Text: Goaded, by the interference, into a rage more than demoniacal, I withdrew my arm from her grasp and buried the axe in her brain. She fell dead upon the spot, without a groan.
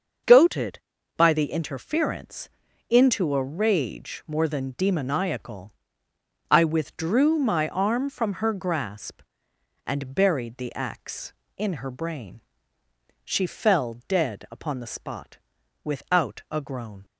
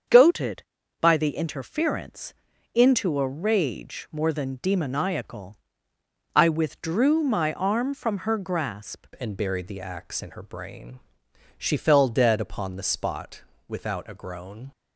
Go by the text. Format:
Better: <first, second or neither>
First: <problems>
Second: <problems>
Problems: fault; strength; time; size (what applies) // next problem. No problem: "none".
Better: first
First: starts louder than the rest; until 1.6 s; 6.5 dB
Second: starts louder than the rest; strong; until 1.4 s; 7 dB // changes voice at "and"; from 9.1 s on; 5.6 s long